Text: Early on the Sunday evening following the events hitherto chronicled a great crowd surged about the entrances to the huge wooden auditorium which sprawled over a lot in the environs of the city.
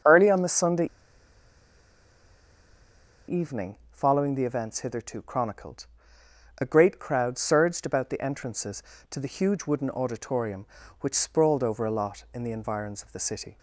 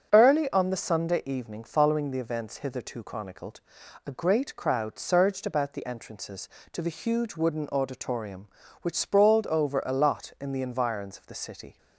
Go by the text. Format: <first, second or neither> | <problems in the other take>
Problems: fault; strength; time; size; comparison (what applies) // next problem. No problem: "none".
second | starts louder than the rest; until 3.4 s; 6.5 dB; also in the second // pauses between "Sunday" and "evening"; strong; at 0.8 s; 2.4 s long // pauses between "evening" and "following"; slight; at 3.7 s; 0.16 s long // pauses between "chronicled" and "a"; noticeable; at 5.8 s; 0.74 s long; also in the second